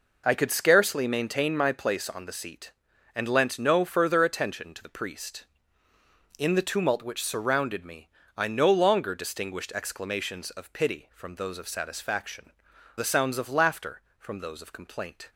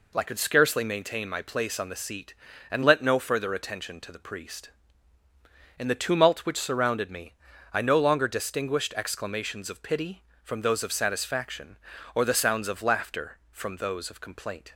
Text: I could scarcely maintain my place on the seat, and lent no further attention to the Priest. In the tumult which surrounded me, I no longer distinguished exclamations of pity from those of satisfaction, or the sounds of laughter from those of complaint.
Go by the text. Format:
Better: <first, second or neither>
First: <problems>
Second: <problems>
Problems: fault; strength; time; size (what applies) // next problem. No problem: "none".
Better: second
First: skips "or"; at 12.7 s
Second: none